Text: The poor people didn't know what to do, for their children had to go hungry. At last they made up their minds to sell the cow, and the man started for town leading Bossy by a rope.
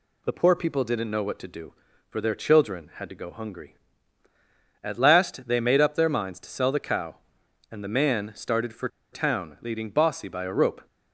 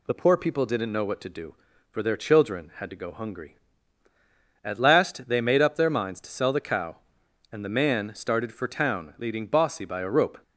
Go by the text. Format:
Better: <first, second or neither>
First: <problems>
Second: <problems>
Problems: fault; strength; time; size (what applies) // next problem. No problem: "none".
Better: second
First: pauses between "for" and "town"; slight; at 8.8 s; 0.25 s long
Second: none